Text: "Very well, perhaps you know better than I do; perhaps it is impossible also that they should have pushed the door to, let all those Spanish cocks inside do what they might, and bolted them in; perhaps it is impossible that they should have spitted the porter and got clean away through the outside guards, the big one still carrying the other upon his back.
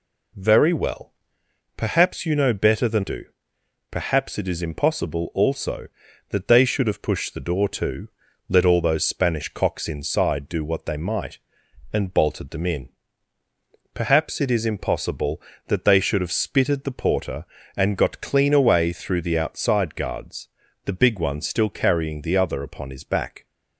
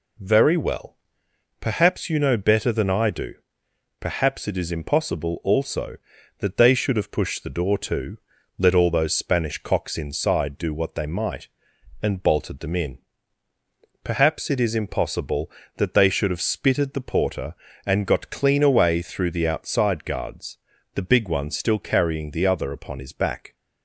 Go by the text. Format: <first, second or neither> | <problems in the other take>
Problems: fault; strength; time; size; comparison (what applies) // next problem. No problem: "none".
second | skips "I"; at 3.0 s